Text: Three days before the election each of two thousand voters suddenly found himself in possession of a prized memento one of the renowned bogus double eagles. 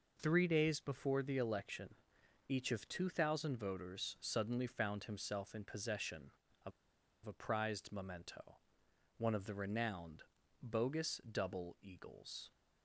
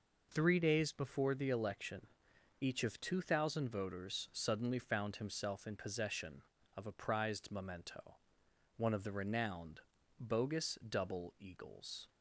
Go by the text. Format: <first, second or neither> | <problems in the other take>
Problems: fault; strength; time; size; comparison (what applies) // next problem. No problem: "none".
second | pauses between "election" and "each"; noticeable; at 1.9 s; 0.54 s long; noticeable in the second // pauses between "of" and "a"; noticeable; at 6.7 s; 0.54 s long // pauses between "memento" and "one"; noticeable; at 8.5 s; 0.60 s long; noticeable in the second // pauses between "renowned" and "bogus"; at 10.2 s; 0.40 s long; also in the second